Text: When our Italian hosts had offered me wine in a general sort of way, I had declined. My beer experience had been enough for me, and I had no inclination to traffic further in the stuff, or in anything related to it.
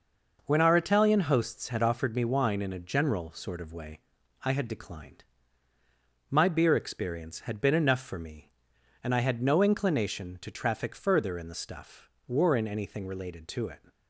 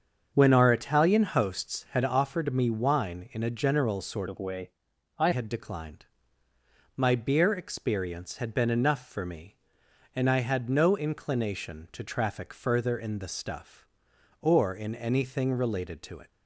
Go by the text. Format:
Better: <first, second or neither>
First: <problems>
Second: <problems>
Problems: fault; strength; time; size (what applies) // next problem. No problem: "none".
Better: first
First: none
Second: starts louder than the rest; until 1.3 s; 7 dB // changes voice from "of" to "I"; from 4.2 to 5.2 s; 1.0 s long